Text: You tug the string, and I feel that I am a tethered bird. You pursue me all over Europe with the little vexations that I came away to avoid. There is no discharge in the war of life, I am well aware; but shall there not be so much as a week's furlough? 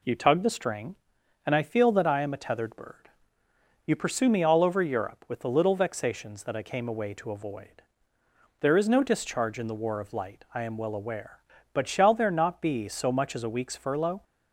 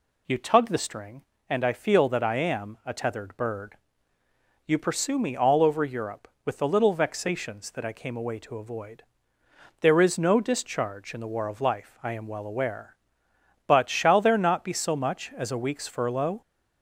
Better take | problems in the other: second | says "light" for "life"; at 10.1 s

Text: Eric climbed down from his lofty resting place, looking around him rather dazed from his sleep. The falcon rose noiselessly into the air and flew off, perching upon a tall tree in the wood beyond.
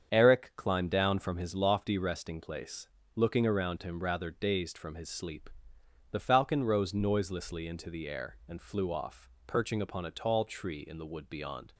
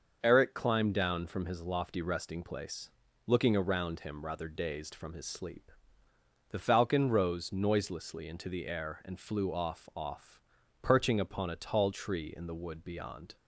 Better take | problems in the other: first | starts louder than the rest; until 1.2 s; 6.5 dB; strong in the first // says "off" twice; at 9.9 s

